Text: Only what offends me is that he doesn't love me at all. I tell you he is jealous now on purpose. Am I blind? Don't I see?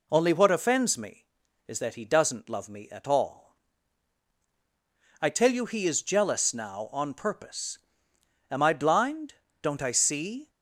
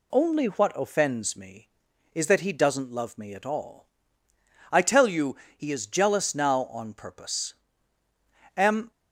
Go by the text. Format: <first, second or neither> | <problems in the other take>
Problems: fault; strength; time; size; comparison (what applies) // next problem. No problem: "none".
first | pauses between "you" and "he"; slight; at 5.3 s; 0.20 s long // stops before "I blind Don't I see"; at 8.9 s